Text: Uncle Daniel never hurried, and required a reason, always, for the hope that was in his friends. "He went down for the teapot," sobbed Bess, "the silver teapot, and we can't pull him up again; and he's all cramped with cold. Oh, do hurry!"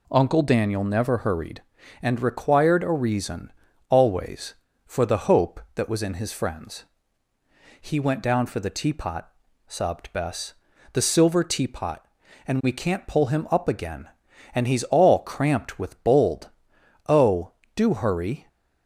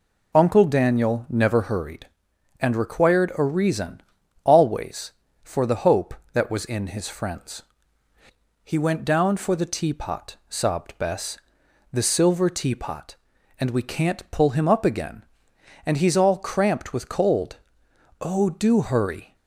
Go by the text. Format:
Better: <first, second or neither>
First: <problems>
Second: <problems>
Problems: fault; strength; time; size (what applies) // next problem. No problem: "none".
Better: second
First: says "bold" for "cold"; at 16.0 s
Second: none